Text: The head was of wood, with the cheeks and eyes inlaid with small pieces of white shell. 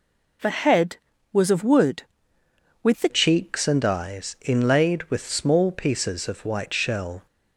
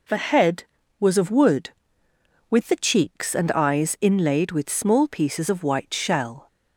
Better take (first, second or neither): second